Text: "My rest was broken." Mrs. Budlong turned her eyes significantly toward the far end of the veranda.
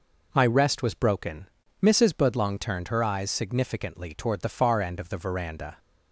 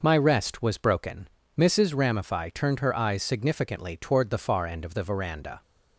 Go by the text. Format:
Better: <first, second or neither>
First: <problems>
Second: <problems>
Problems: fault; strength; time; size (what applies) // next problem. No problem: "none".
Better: first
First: none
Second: says "Ramify" for "Budlong"; at 1.9 s